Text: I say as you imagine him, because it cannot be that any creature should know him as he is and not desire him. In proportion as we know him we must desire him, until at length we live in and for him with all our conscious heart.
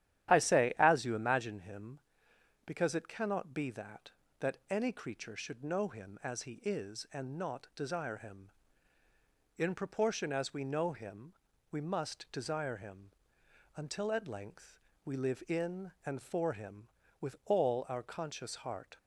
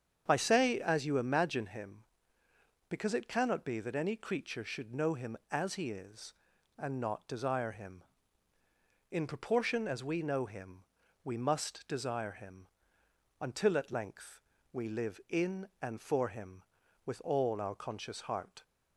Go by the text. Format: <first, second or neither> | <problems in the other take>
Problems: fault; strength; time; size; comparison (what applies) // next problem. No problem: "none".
second | starts louder than the rest; strong; until 1.3 s; 11.5 dB; strong in the second // says "that" twice; at 4.4 s // pauses between "him" and "we"; at 11.3 s; 0.38 s long; also in the second // pauses between "length" and "we"; slight; at 14.7 s; 0.24 s long; slight in the second